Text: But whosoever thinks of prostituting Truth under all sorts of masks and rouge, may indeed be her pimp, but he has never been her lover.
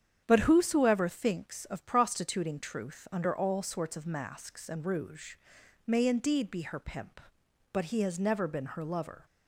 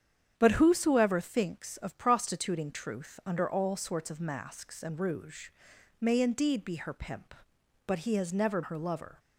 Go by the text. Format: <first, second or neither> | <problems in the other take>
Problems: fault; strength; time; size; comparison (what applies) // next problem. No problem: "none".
first | starts louder than the rest; strong; until 1.3 s; 8.5 dB; strong in the first // skips "been"; at 8.6 s